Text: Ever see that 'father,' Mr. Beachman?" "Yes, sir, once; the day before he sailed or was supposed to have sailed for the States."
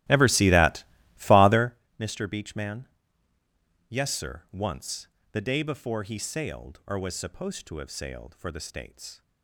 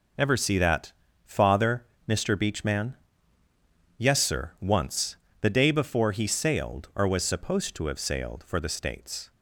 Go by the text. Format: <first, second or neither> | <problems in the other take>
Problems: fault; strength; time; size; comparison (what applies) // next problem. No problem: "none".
second | starts louder than the rest; strong; until 1.8 s; 16 dB // pauses between "that" and "father"; slight; at 0.8 s; 0.34 s long; slight in the second